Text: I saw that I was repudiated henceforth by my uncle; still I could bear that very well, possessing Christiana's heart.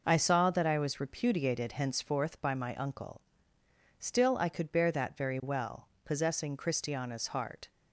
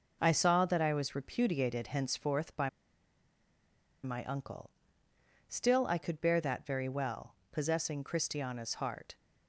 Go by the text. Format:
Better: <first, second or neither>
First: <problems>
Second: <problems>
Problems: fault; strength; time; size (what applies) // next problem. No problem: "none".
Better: first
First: none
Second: pauses between "by" and "my"; strong; at 2.6 s; 1.3 s long